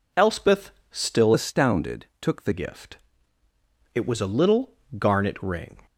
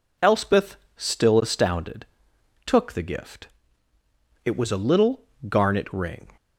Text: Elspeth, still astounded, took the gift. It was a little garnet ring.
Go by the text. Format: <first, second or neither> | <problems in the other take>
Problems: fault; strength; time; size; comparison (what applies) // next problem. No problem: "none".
second | changes voice from "astounded" to "the"; from 1.3 to 2.5 s; 1.2 s long // pauses between "little" and "garnet"; slight; at 4.7 s; 0.24 s long; slight in the second